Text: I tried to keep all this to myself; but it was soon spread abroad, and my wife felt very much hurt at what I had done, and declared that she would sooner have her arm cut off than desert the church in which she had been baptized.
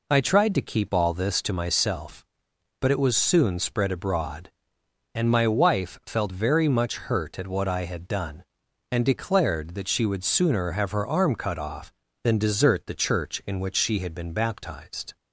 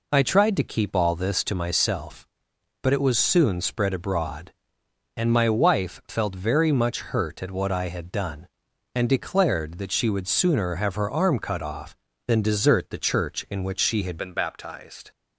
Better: first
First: none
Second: changes voice at "been"; from 14.1 s on; 0.9 s long

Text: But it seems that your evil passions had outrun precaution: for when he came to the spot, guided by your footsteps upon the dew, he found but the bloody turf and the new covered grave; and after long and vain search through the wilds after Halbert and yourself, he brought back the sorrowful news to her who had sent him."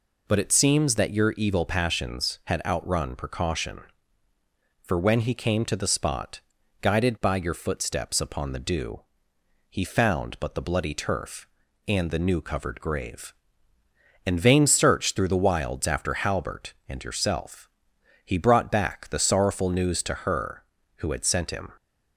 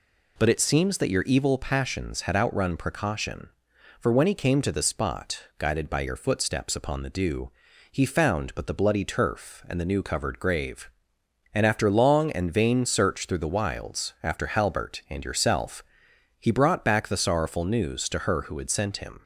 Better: second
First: skips "after long and"; at 14.4 s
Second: none

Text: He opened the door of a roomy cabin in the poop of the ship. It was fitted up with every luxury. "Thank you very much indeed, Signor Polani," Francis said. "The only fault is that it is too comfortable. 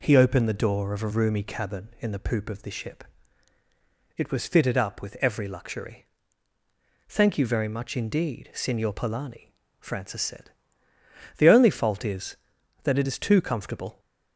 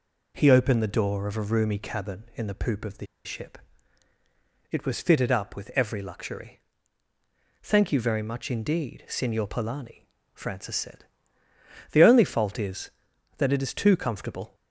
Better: first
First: none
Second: pauses between "the" and "ship"; slight; at 3.0 s; 0.19 s long

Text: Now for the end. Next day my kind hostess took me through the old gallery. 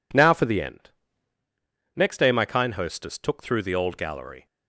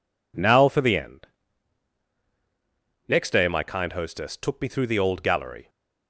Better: second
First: skips "me"; at 3.4 s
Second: none

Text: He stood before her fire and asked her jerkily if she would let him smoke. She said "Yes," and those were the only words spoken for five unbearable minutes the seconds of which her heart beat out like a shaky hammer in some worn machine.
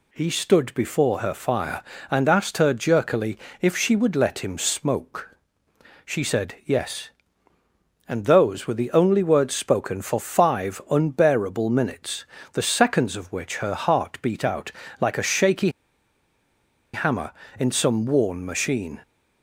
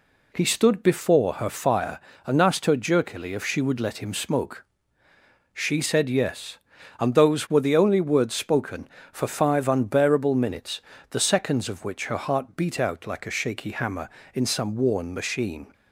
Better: second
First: pauses between "jerkily" and "if"; slight; at 3.3 s; 0.22 s long // pauses between "minutes" and "the"; slight; at 12.2 s; 0.28 s long // pauses between "out" and "like"; slight; at 14.7 s; 0.26 s long // pauses between "shaky" and "hammer"; at 15.6 s; 1.2 s long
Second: pauses between "minutes" and "the"; slight; at 10.8 s; 0.30 s long

